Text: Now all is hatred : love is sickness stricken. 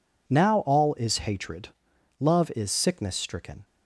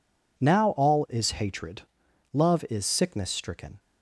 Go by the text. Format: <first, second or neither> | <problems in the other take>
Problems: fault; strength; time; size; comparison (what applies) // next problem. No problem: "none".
neither | none